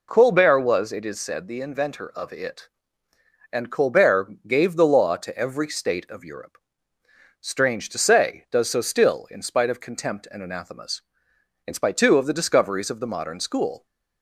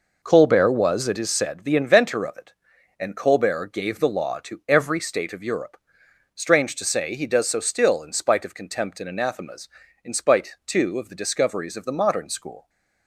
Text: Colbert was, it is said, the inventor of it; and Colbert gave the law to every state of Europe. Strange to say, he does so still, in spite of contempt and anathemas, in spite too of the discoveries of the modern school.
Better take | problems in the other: second | skips "he"; at 8.4 s

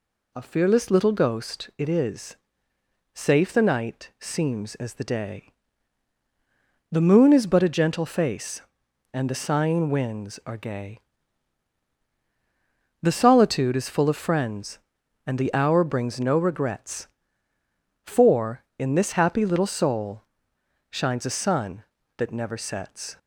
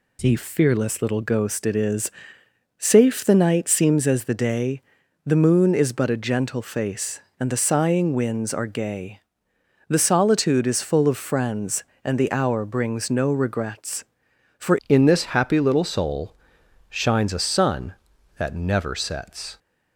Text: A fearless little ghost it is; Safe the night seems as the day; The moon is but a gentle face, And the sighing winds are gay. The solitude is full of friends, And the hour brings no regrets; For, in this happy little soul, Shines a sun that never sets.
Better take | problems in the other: first | changes voice at "in"; from 14.8 s on; 4.7 s long

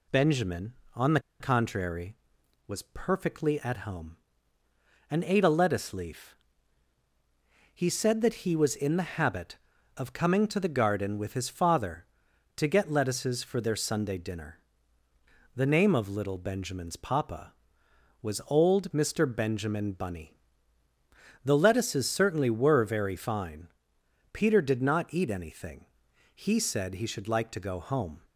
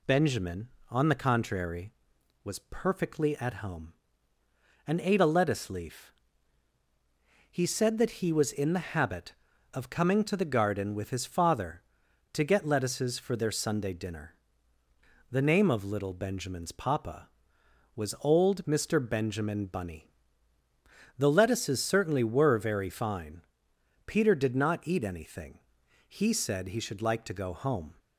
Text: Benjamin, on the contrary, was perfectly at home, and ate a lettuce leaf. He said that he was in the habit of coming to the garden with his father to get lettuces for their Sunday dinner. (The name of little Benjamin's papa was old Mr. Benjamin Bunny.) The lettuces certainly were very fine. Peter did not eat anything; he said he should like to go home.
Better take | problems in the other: second | pauses between "the" and "contrary"; slight; at 1.1 s; 0.20 s long

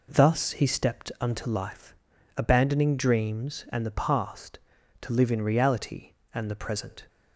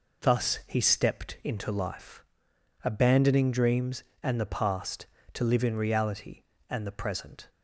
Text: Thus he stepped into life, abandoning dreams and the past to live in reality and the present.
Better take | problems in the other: second | says "unto" for "into"; at 1.2 s

